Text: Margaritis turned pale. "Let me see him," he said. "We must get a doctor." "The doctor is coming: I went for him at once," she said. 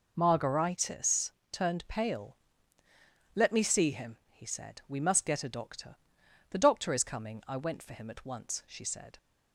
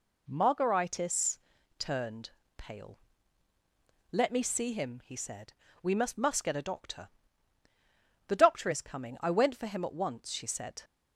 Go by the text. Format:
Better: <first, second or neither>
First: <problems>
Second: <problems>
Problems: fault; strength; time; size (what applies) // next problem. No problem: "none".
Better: first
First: pauses between "Margaritis" and "turned"; slight; at 1.3 s; 0.20 s long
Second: pauses between "Margaritis" and "turned"; at 1.3 s; 0.40 s long // pauses between "turned" and "pale"; slight; at 2.2 s; 0.26 s long // says "must" twice; at 6.1 s